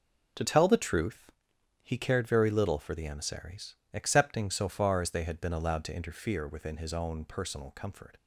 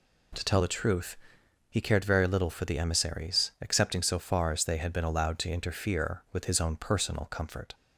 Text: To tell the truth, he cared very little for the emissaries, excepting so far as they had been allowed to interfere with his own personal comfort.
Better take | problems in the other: second | says "within" for "with"; at 6.4 s

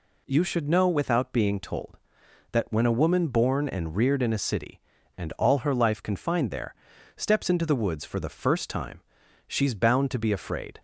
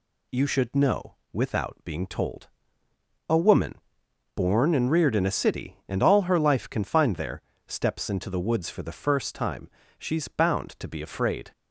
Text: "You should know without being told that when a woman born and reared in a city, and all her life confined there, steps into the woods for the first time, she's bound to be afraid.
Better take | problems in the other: first | pauses between "know" and "without"; slight; at 1.1 s; 0.18 s long // skips "that when"; at 2.8 s // pauses between "woman" and "born"; noticeable; at 3.7 s; 0.62 s long

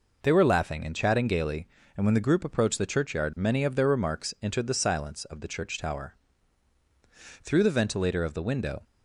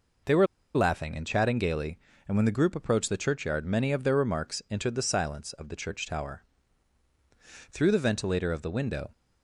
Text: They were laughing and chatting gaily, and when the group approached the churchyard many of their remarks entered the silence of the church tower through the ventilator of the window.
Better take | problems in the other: first | pauses between "were" and "laughing"; slight; at 0.4 s; 0.29 s long // pauses between "tower" and "through"; strong; at 6.4 s; 1.2 s long; strong in the first

